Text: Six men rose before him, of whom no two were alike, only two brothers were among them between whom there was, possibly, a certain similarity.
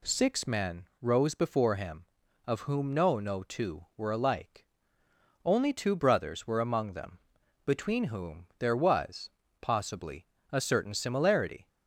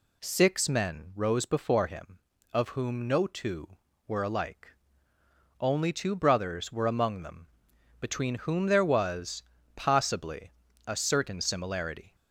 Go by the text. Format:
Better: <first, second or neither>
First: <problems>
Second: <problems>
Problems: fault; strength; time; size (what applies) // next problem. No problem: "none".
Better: second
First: pauses between "men" and "rose"; slight; at 0.8 s; 0.16 s long // says "no" twice; at 3.1 s // pauses between "them" and "between"; at 7.1 s; 0.44 s long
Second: pauses between "them" and "between"; noticeable; at 7.4 s; 0.54 s long